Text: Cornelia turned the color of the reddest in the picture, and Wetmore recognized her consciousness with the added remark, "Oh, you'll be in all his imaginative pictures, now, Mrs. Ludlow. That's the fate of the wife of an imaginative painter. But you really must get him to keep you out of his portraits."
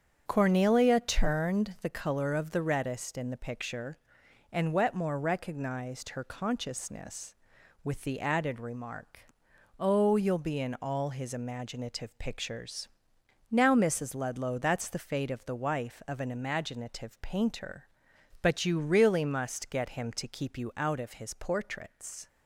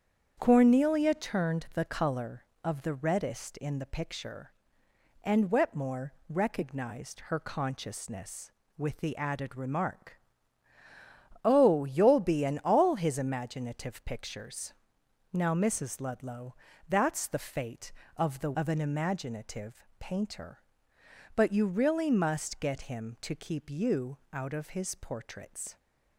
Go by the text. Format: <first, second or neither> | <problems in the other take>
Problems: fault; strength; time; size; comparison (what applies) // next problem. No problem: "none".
first | starts louder than the rest; strong; until 1.3 s; 8 dB; strong in the first // pauses between "Wetmore" and "recognized"; slight; at 6.1 s; 0.16 s long // skips "wife"; at 18.5 s // pauses between "imaginative" and "painter"; slight; at 19.8 s; 0.16 s long